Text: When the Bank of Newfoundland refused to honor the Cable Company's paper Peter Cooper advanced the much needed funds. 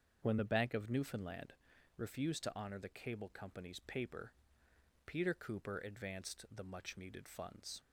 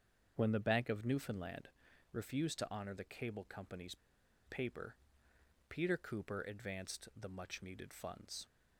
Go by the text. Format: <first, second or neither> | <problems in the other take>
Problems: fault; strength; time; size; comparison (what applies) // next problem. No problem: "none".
first | starts louder than the rest; until 1.3 s; 7 dB; also in the first // pauses between "Newfoundland" and "refused"; at 1.6 s; 0.44 s long; also in the first // pauses between "Company's" and "paper"; noticeable; at 3.9 s; 0.50 s long // pauses between "paper" and "Peter"; noticeable; at 4.9 s; 0.72 s long; noticeable in the first